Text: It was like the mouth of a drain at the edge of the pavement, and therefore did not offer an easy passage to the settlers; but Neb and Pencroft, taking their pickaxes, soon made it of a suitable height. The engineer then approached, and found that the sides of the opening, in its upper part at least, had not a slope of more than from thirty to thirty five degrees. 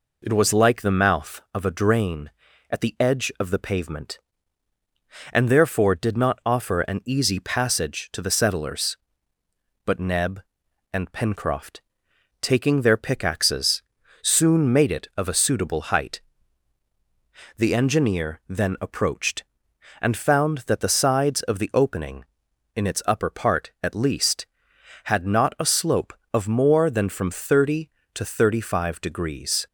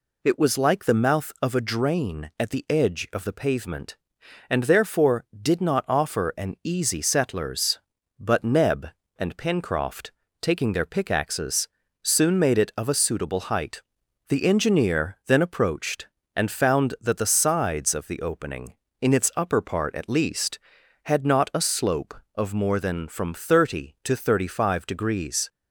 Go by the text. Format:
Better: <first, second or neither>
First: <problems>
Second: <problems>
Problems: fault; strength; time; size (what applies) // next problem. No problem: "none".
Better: first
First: none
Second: skips "passage to the"; at 6.9 s